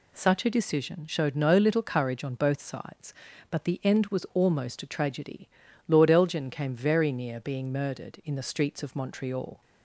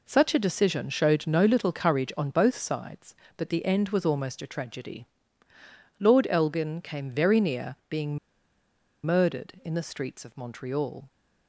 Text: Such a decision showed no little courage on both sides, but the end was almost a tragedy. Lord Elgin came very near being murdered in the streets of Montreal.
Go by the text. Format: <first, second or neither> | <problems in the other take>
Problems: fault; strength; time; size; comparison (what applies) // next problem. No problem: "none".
first | pauses between "being" and "murdered"; noticeable; at 8.1 s; 0.86 s long